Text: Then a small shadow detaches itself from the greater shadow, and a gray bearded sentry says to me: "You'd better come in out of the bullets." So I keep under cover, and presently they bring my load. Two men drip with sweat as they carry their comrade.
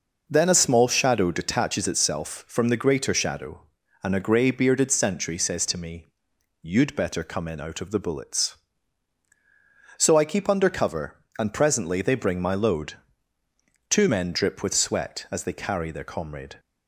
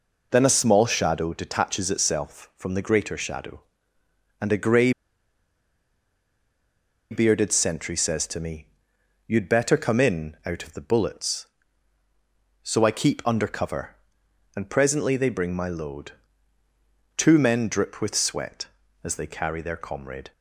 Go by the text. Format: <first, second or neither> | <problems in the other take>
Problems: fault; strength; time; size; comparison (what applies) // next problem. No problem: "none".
first | pauses between "gray" and "bearded"; strong; at 4.9 s; 2.1 s long